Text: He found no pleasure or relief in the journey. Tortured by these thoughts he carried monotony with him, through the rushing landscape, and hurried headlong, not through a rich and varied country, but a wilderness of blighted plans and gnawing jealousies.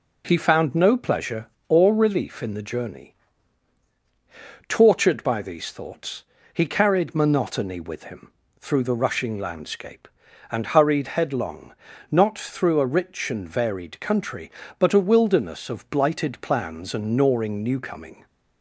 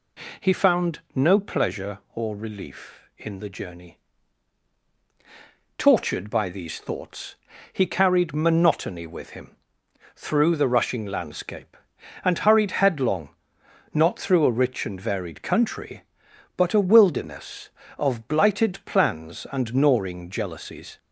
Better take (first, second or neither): second